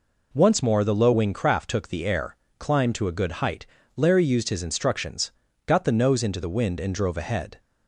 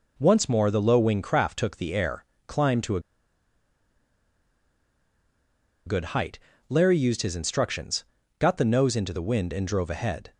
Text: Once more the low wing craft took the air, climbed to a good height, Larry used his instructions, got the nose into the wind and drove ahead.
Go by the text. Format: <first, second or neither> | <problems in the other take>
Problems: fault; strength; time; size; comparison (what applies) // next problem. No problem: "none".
first | pauses between "a" and "good"; strong; at 3.0 s; 2.8 s long